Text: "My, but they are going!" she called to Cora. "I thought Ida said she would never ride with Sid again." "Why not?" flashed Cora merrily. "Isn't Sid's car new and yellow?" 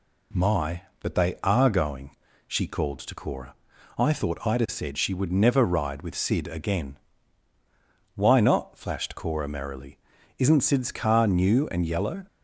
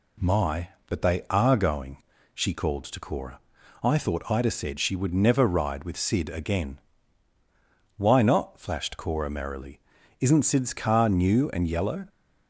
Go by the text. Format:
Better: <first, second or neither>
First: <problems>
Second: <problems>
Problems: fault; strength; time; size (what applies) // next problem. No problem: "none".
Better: neither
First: none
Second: none